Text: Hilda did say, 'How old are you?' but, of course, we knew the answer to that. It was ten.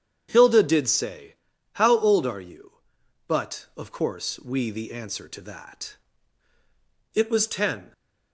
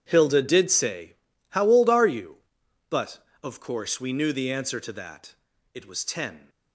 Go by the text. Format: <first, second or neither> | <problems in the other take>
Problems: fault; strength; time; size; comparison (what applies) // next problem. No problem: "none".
second | starts louder than the rest; strong; until 1.3 s; 8.5 dB // skips "knew"; at 4.6 s